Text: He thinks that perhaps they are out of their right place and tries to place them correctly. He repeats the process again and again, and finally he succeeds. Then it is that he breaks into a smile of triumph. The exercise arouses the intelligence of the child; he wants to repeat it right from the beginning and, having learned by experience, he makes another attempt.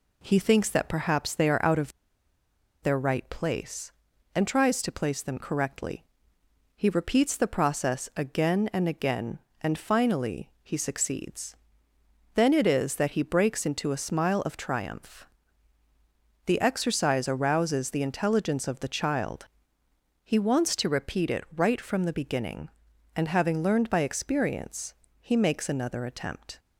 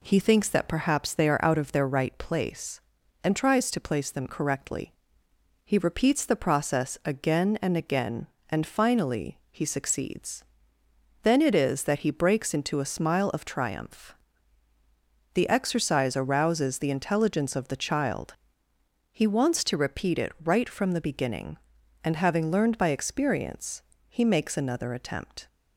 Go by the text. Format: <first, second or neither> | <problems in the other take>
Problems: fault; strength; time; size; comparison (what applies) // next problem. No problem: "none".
second | pauses between "of" and "their"; noticeable; at 1.9 s; 0.91 s long